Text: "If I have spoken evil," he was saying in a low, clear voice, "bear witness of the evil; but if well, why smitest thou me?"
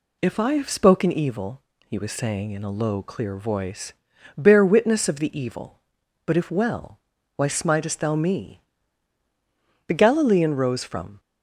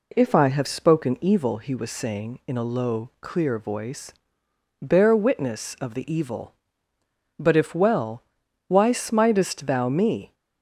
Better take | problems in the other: second | goes on to say "The Galilean rose from"; from 9.8 s on; 1.3 s long

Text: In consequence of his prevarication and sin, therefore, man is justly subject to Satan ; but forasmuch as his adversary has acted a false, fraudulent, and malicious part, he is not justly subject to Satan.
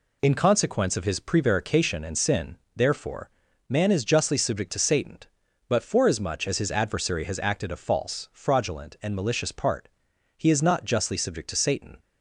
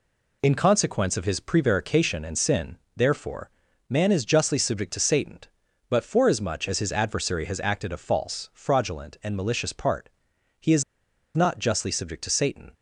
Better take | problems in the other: first | pauses between "is" and "not"; noticeable; at 10.8 s; 0.53 s long

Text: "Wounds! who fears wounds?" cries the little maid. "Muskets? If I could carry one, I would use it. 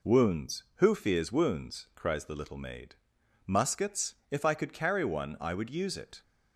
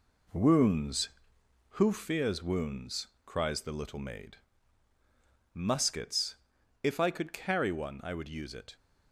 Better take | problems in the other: first | gets quieter; throughout; 6.5 dB

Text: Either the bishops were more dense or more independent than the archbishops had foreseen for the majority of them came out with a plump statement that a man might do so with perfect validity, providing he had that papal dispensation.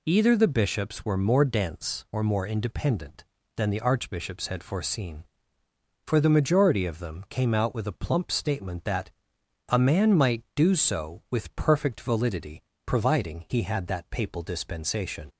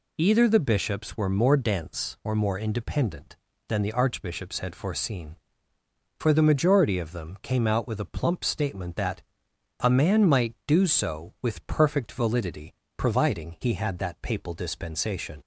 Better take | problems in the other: neither | pauses between "that" and "a"; noticeable; the same in both

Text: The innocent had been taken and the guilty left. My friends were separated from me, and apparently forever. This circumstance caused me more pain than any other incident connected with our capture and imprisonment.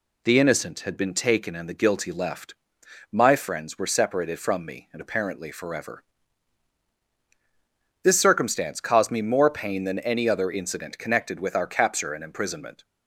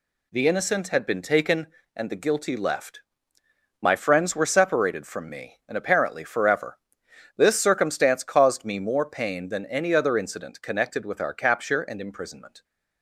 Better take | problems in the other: neither | none

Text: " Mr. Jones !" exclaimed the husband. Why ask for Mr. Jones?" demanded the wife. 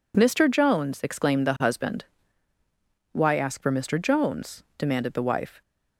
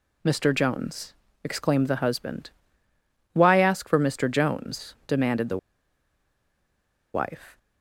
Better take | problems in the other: first | pauses between "the" and "wife"; strong; at 5.5 s; 1.5 s long

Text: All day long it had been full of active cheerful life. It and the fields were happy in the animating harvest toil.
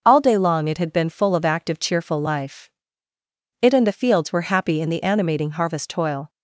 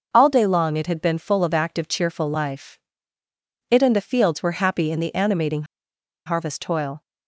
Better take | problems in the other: first | starts louder than the rest; noticeable; until 1.1 s; 6 dB; noticeable in the first // pauses between "animating" and "harvest"; noticeable; at 5.6 s; 0.62 s long

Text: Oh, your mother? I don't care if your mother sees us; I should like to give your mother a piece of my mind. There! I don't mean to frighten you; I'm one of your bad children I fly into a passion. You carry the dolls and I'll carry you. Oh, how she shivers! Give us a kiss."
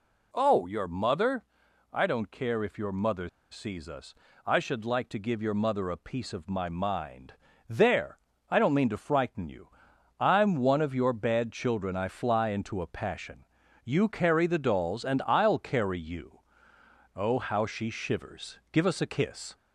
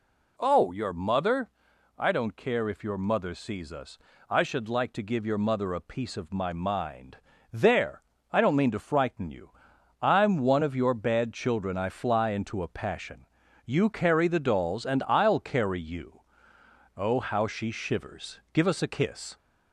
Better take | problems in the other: second | pauses between "mother" and "sees"; slight; at 3.2 s; 0.24 s long

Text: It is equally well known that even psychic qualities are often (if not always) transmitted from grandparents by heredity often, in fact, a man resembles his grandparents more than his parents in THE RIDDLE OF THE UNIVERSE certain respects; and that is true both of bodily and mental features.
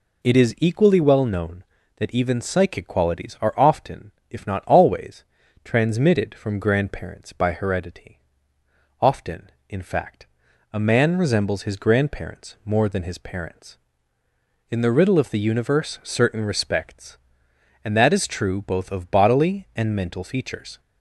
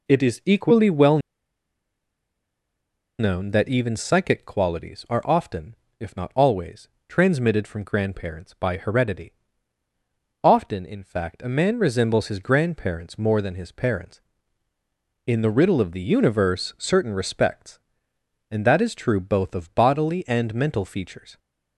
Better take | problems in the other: first | pauses between "well" and "known"; strong; at 1.1 s; 2.0 s long // pauses between "heredity" and "often"; at 9.3 s; 1.1 s long; noticeable in the first

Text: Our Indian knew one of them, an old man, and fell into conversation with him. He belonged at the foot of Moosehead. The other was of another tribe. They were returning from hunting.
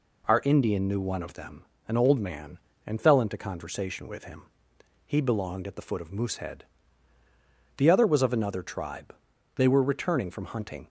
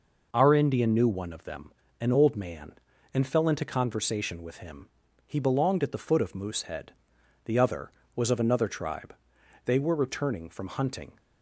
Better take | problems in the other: neither | none

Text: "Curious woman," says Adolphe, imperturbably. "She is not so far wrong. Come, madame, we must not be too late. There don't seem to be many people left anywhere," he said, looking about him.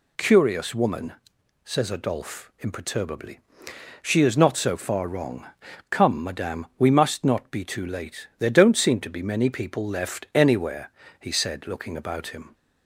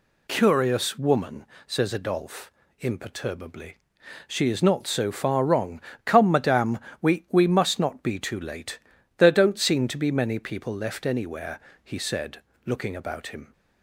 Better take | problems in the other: first | says "we" twice; at 7.3 s

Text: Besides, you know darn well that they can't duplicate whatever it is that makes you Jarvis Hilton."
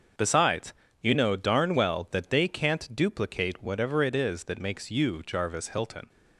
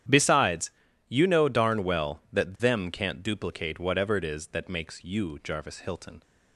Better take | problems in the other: first | starts louder than the rest; strong; until 1.4 s; 10.5 dB; also in the first // says "them" for "they"; at 2.5 s

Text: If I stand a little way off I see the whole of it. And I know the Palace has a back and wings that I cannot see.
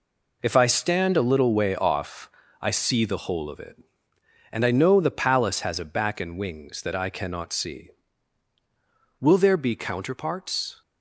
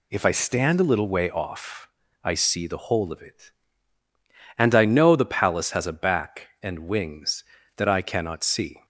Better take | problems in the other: second | pauses between "off" and "I"; slight; at 2.2 s; 0.32 s long; slight in the second // goes on to say "Will there be counterparts"; from 9.1 s on; 1.6 s long

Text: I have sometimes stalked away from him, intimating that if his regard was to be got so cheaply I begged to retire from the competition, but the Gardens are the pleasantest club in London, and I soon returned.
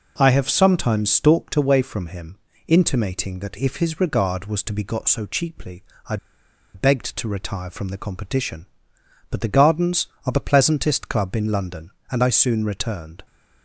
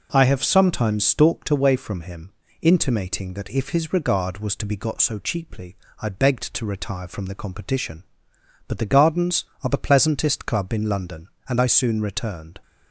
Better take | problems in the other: second | pauses between "cheaply" and "I"; slight; at 5.8 s; 0.26 s long; slight in the second // pauses between "I" and "begged"; noticeable; at 6.1 s; 0.57 s long

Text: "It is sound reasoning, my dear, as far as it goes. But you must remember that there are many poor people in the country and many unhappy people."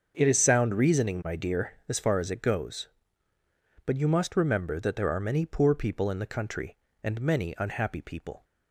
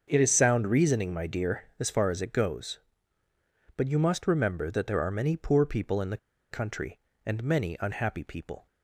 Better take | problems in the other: first | starts louder than the rest; until 1.0 s; 6.5 dB; also in the first // pauses between "the" and "country"; slight; at 6.1 s; 0.34 s long

